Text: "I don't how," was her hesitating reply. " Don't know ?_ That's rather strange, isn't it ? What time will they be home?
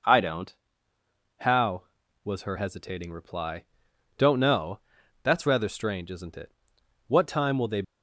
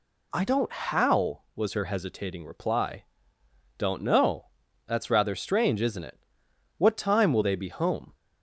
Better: second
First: pauses between "don't" and "how"; noticeable; at 0.5 s; 0.84 s long // stops before "be home"; at 7.8 s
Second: none

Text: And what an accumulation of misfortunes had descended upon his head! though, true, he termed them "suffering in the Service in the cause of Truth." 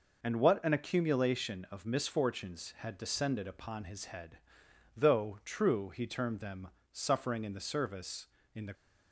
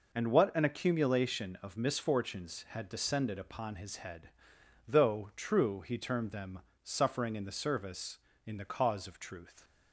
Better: second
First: pauses between "them" and "suffering"; slight; at 6.6 s; 0.22 s long // stops before "cause of Truth"; at 8.7 s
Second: pauses between "them" and "suffering"; slight; at 6.5 s; 0.22 s long

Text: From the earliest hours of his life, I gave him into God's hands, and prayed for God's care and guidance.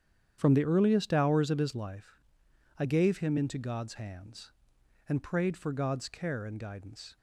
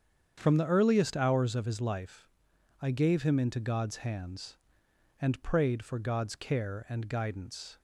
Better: neither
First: starts louder than the rest; strong; until 1.4 s; 9 dB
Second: starts louder than the rest; strong; until 1.3 s; 8 dB

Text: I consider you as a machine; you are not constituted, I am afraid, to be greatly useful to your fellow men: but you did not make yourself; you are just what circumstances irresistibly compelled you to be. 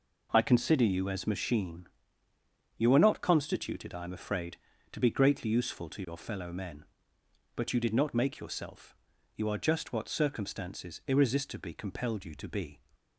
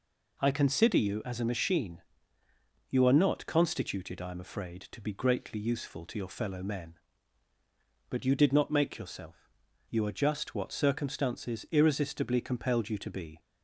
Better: second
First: skips "a"; at 1.2 s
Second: none

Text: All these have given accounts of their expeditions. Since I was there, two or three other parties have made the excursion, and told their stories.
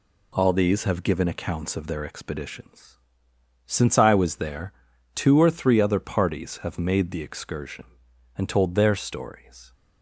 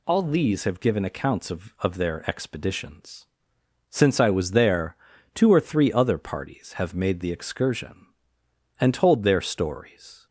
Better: first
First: none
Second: says "of" twice; at 1.7 s

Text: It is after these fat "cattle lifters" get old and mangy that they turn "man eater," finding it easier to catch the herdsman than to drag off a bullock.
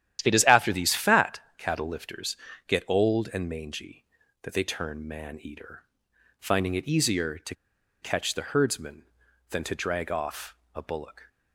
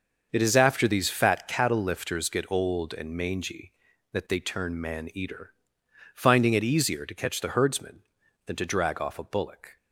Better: second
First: starts louder than the rest; strong; until 1.2 s; 11 dB // pauses between "fat" and "cattle"; slight; at 1.4 s; 0.16 s long // pauses between "lifters" and "get"; slight; at 2.3 s; 0.30 s long // pauses between "to" and "catch"; noticeable; at 7.5 s; 0.47 s long // pauses between "off" and "a"; slight; at 10.5 s; 0.18 s long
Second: starts louder than the rest; until 1.3 s; 6.5 dB

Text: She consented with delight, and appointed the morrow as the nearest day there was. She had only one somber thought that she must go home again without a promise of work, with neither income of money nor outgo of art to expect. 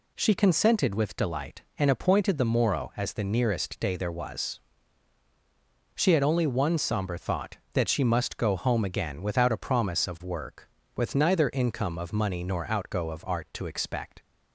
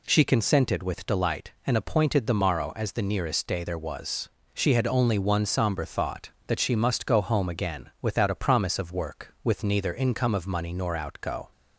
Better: first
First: none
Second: stops before "of art to expect"; at 11.5 s

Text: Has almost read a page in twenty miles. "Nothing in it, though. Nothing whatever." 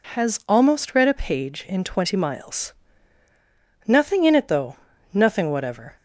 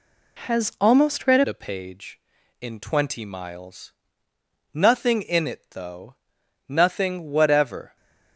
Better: first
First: none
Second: changes voice at "a"; from 1.4 s on; 6.5 s long

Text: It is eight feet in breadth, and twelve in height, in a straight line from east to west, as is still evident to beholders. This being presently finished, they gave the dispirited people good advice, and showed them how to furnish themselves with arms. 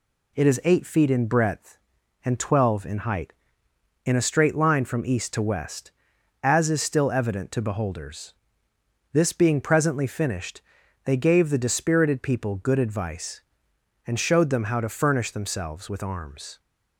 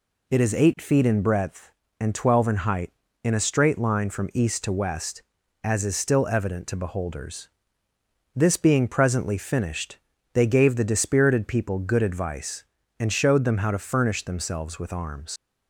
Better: first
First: none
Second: leaves "arms" unfinished; at 15.3 s; 95 ms

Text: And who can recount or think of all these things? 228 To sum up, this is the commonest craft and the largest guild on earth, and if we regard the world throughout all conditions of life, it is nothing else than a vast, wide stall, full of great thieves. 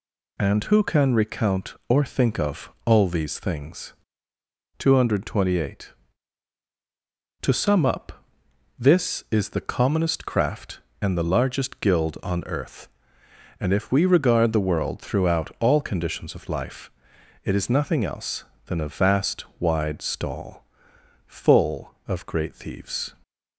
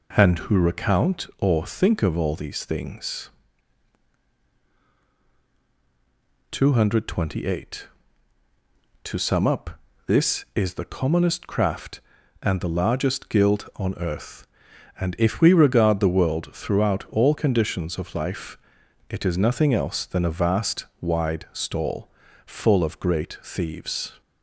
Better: first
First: none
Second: skips "can"; at 0.5 s

